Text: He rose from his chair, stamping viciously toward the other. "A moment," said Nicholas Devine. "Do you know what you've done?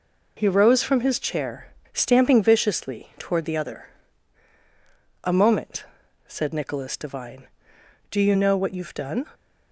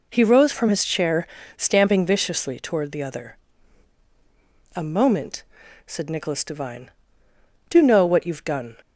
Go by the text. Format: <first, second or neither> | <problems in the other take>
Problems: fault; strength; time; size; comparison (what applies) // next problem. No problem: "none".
first | skips "you"; at 7.8 s